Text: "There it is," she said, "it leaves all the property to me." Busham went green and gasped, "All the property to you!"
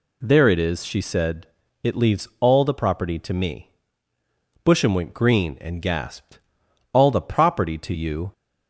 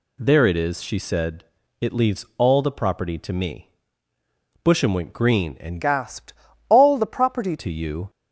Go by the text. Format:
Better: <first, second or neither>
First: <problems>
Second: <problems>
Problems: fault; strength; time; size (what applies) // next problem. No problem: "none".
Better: first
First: none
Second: changes voice from "gasped" to "property"; from 5.8 to 7.5 s; 1.7 s long